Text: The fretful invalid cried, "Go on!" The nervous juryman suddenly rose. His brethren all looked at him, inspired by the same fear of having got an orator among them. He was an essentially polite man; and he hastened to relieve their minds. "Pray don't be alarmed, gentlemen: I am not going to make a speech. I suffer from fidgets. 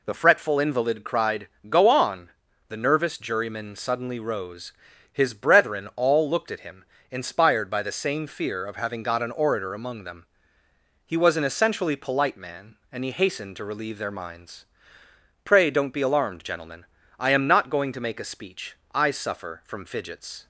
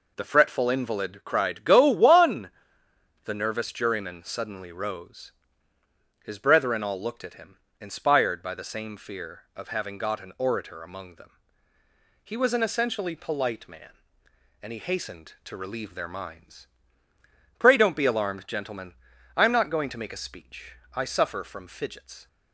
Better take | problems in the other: first | says "one" for "on"; at 1.8 s

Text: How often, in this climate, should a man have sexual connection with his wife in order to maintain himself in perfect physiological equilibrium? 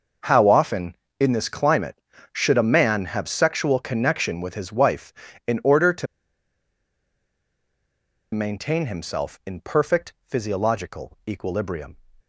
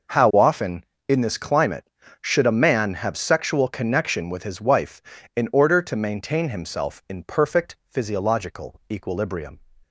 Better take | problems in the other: second | pauses between "to" and "maintain"; strong; at 6.0 s; 2.2 s long // pauses between "perfect" and "physiological"; slight; at 10.1 s; 0.16 s long; slight in the second

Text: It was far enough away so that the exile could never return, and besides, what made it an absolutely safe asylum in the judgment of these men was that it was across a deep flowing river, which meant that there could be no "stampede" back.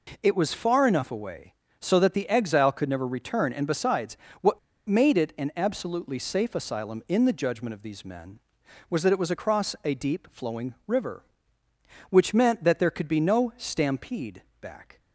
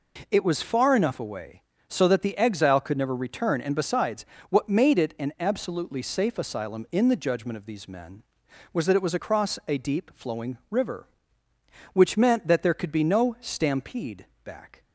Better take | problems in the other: second | pauses between "what" and "made"; slight; at 4.5 s; 0.28 s long // pauses between "stampede" and "back"; slight; at 14.4 s; 0.18 s long; slight in the second

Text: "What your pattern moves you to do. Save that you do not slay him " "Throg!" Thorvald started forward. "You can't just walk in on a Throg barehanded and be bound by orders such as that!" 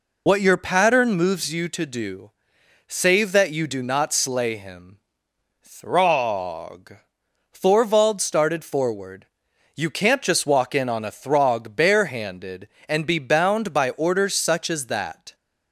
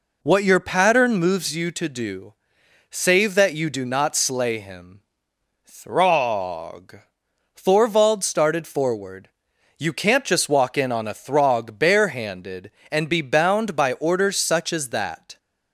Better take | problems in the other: second | loses the start of "What"; at 0.2 s; 55 ms

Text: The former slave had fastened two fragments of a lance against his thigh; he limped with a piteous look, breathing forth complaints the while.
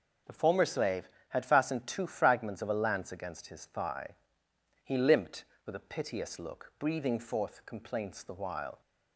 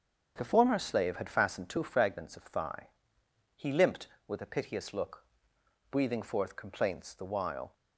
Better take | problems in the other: first | starts louder than the rest; until 1.3 s; 7 dB // skips "a lance against his"; at 2.4 s

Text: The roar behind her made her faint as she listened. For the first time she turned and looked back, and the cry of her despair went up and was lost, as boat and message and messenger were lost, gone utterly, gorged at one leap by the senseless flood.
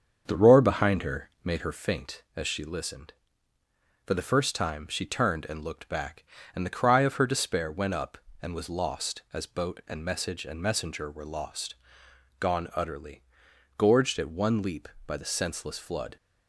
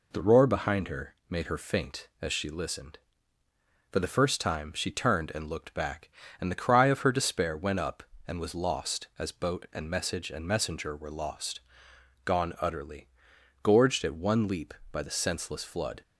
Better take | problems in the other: second | starts louder than the rest; strong; until 1.7 s; 7 dB // pauses between "her" and "made"; slight; at 1.2 s; 0.16 s long; slight in the second

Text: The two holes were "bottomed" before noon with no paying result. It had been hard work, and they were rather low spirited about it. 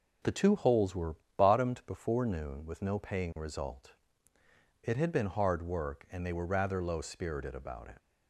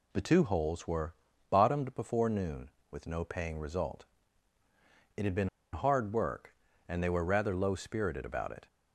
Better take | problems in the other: first | pauses between "were" and "bottomed"; slight; at 1.1 s; 0.36 s long; slight in the first // pauses between "been" and "hard"; slight; at 5.4 s; 0.24 s long

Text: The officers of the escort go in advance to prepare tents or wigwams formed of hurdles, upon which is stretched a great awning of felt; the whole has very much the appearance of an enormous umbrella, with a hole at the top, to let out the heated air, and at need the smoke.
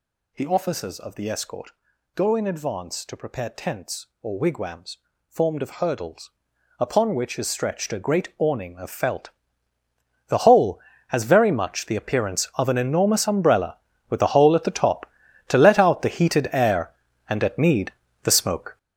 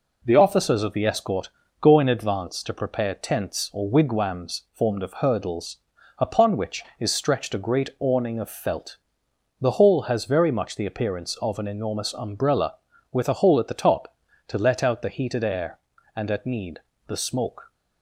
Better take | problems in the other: second | gets louder; strong; throughout; 10 dB // pauses between "escort" and "go"; at 1.7 s; 0.44 s long; slight in the second // pauses between "wigwams" and "formed"; slight; at 4.9 s; 0.32 s long // pauses between "need" and "the"; slight; at 17.9 s; 0.32 s long; slight in the second

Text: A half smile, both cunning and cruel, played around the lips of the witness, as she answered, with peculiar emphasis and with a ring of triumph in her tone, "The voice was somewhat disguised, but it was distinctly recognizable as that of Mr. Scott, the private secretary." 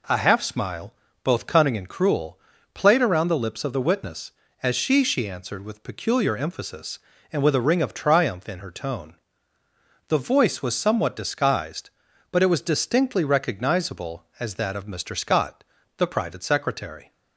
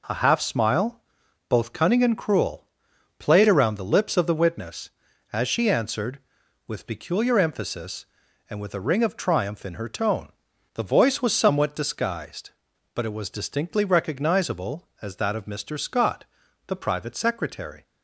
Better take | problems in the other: second | says "she" twice; at 5.0 s

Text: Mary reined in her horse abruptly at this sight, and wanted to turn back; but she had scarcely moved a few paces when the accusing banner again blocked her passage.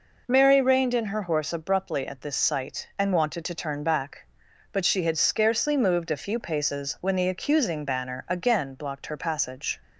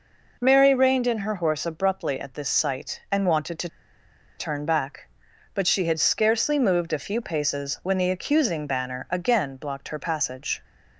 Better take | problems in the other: first | pauses between "to" and "turn"; noticeable; at 3.6 s; 0.70 s long

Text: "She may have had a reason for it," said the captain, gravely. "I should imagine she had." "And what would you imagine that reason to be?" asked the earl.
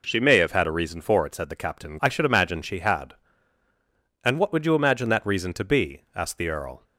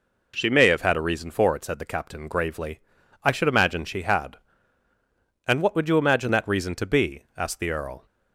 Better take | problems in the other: second | skips "gravely"; at 1.9 s

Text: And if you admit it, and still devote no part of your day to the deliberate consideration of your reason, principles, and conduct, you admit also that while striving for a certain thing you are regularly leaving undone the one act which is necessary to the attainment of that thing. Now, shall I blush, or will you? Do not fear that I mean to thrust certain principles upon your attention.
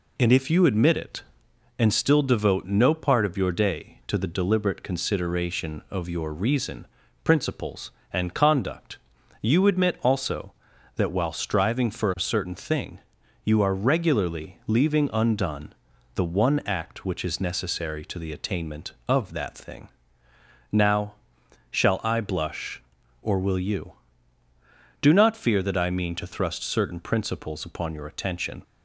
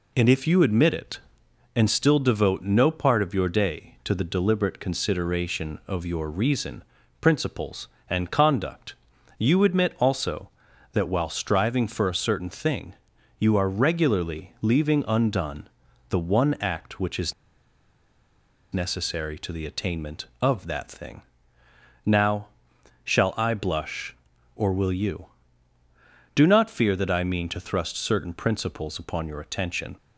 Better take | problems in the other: first | pauses between "thing" and "you"; noticeable; at 12.9 s; 0.46 s long; noticeable in the first // pauses between "undone" and "the"; at 15.6 s; 0.40 s long; also in the first // pauses between "is" and "necessary"; strong; at 17.3 s; 1.3 s long

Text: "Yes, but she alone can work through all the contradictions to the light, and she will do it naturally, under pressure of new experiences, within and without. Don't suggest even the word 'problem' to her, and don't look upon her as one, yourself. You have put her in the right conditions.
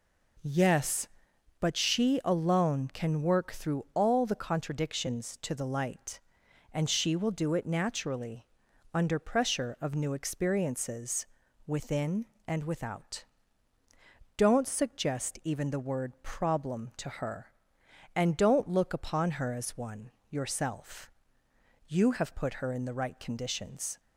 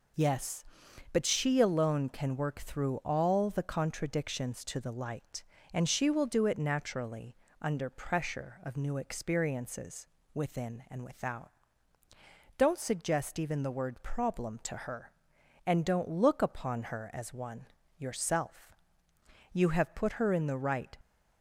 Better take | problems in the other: first | stops before "conditions"; at 21.0 s

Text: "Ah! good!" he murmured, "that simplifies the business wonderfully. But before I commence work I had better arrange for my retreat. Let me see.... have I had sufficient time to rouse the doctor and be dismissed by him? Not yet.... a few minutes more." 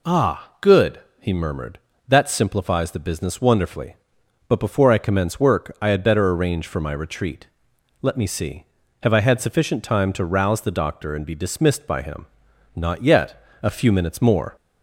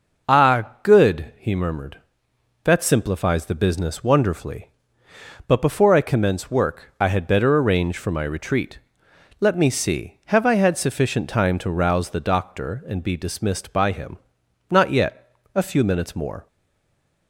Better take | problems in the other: first | stays silent after the last word; slight; from 16.4 s on; 0.8 s long

